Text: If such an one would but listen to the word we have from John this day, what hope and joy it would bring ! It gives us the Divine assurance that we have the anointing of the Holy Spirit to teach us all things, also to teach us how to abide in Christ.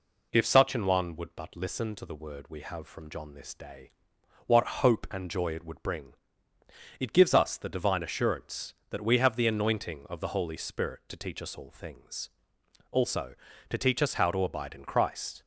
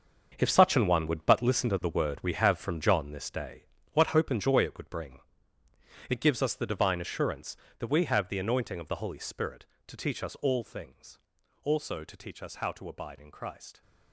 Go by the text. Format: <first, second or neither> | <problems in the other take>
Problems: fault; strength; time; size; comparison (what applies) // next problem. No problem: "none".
first | gets quieter; strong; throughout; 13 dB